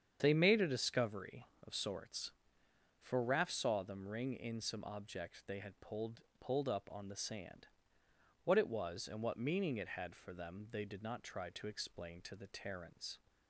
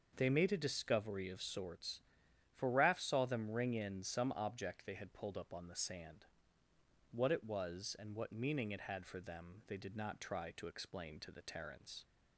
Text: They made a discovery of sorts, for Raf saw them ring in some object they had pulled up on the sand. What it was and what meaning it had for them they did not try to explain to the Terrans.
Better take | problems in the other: second | starts louder than the rest; strong; until 1.2 s; 8 dB; noticeable in the second // says "pulled" twice; at 6.3 s

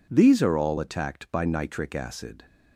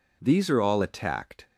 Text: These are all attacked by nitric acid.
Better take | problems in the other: first | stops before "by nitric acid"; at 1.4 s

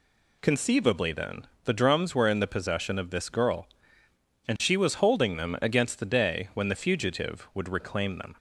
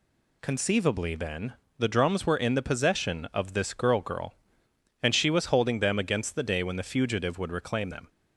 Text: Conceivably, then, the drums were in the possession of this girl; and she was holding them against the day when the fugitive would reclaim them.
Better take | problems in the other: first | says "girl" twice; at 4.0 s

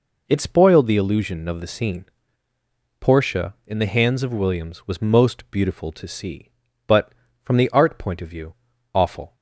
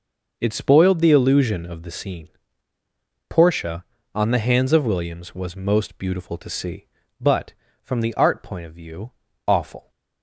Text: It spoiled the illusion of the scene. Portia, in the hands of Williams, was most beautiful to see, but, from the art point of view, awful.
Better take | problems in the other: first | says "on" for "in"; at 4.1 s

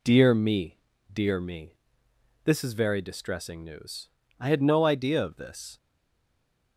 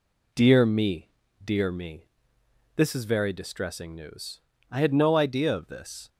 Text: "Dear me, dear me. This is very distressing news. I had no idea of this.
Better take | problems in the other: second | stays silent after the last word; from 5.7 s on; 1.0 s long

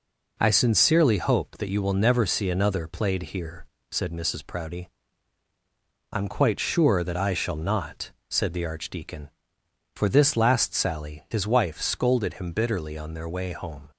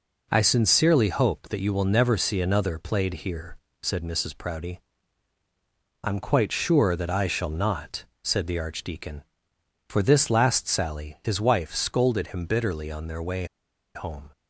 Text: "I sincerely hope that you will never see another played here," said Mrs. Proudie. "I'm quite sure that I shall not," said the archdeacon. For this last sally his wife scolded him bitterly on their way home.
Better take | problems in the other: first | pauses between "way" and "home"; noticeable; at 13.4 s; 0.48 s long

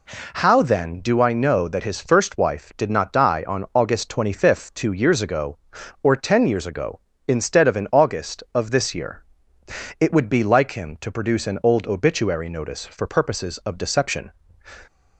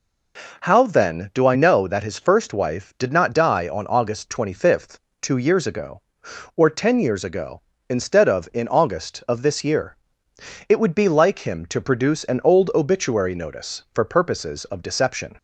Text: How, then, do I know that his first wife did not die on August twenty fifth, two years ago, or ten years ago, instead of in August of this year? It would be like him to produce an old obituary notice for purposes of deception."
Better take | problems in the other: neither | none

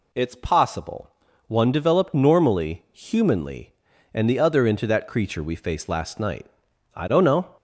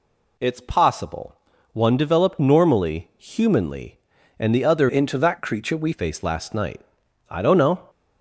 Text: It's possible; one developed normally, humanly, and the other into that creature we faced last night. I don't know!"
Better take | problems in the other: first | changes voice from "into" to "we"; from 4.8 to 5.9 s; 1.1 s long

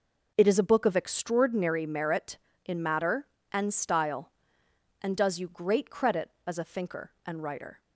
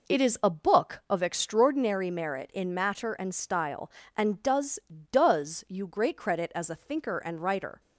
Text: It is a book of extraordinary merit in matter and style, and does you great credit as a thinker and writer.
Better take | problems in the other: first | says "does" twice; at 5.0 s

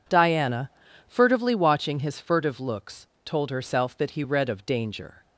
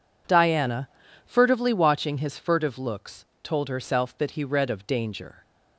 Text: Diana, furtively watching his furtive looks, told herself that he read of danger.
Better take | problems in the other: neither | none

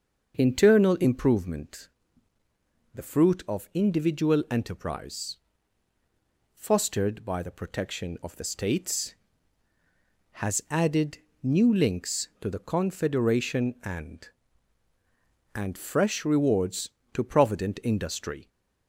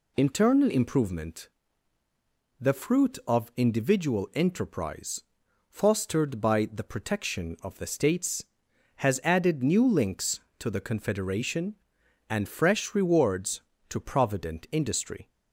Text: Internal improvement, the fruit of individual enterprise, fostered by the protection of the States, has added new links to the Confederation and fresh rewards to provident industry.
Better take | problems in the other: second | starts louder than the rest; until 1.3 s; 6.5 dB // pauses between "added" and "new"; slight; at 11.1 s; 0.24 s long // says "and" twice; at 15.5 s

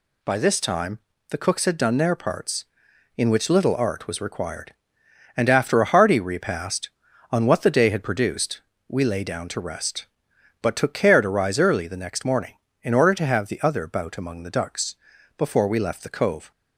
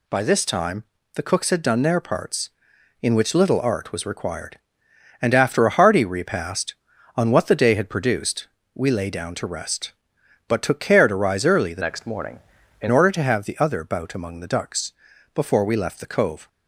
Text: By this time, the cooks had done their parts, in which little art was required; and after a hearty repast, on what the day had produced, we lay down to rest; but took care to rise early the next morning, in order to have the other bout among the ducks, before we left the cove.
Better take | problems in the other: first | changes voice from "next" to "in"; from 11.8 to 12.8 s; 1.0 s long

